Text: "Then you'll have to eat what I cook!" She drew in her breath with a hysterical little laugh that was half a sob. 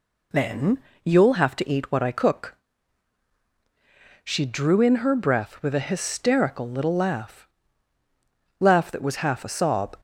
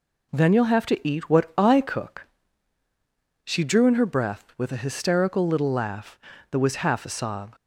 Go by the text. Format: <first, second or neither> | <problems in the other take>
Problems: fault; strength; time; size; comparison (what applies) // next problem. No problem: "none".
second | pauses between "Then" and "you'll"; slight; at 0.8 s; 0.22 s long // says "laugh" twice; at 8.5 s